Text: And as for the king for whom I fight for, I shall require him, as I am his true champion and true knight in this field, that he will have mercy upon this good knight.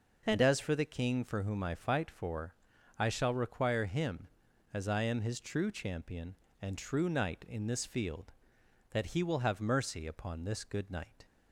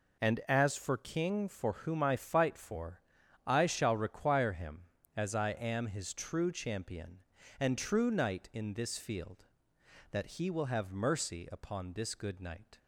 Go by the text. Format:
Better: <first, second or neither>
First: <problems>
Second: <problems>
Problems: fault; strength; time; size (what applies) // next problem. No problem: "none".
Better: first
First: none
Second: skips "the"; at 0.9 s